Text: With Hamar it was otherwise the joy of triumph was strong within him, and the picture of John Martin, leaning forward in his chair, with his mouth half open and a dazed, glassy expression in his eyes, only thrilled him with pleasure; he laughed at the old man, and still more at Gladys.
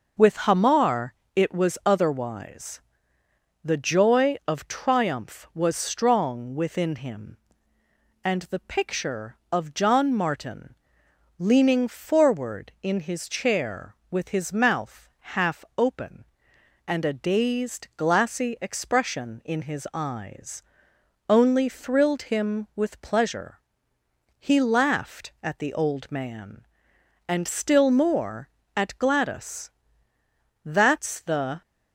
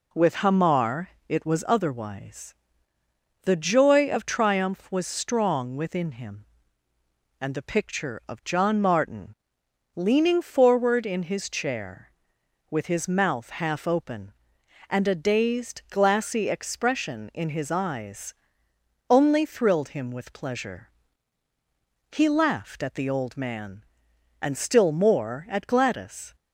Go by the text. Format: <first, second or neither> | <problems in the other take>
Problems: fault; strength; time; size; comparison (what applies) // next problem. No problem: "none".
second | pauses between "Hamar" and "it"; slight; at 1.1 s; 0.22 s long; slight in the second // pauses between "otherwise" and "the"; noticeable; at 2.7 s; 0.84 s long; noticeable in the second // goes on to say "That's the"; noticeable; from 30.6 s on; 0.98 s long